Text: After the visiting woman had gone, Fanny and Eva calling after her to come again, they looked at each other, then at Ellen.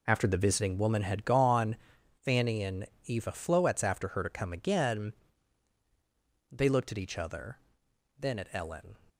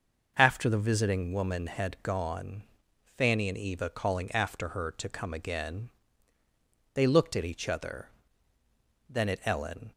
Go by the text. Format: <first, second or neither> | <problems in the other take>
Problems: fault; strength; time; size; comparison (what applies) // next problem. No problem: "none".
second | pauses between "and" and "Eva"; slight; at 2.8 s; 0.20 s long // says "floetz" for "calling"; at 3.3 s